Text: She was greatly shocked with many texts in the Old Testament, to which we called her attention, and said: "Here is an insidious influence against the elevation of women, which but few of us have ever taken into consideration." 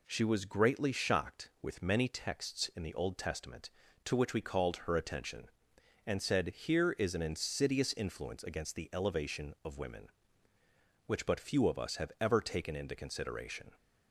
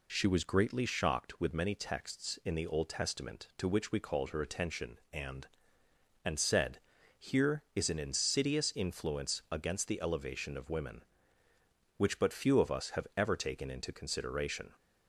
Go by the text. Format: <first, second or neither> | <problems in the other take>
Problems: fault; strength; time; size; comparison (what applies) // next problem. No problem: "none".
first | says "and" twice; at 6.2 s